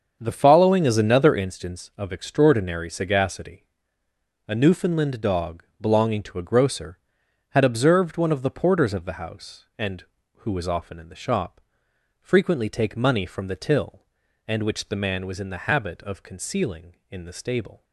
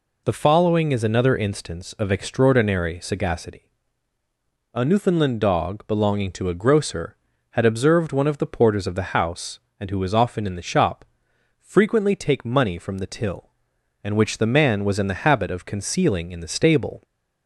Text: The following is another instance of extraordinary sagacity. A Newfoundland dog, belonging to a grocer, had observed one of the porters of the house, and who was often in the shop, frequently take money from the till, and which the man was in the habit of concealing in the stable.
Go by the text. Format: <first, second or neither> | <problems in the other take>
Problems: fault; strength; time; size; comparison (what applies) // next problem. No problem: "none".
second | starts louder than the rest; until 1.5 s; 7 dB